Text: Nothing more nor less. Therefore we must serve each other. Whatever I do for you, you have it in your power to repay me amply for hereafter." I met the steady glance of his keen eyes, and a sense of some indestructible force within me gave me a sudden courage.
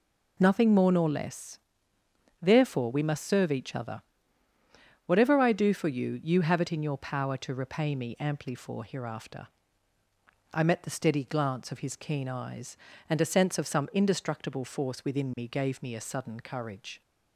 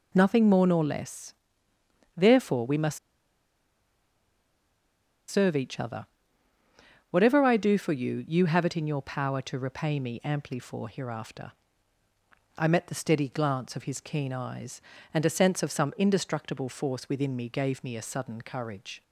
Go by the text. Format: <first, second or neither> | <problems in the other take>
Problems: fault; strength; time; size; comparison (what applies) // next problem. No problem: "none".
first | pauses between "must" and "serve"; strong; at 2.9 s; 2.3 s long